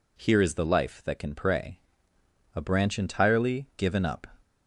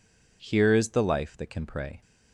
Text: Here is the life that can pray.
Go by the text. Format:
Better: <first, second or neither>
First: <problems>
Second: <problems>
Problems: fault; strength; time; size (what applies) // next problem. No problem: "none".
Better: second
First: goes on to say "A branch entirely given up"; strong; from 2.5 s on; 1.7 s long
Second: none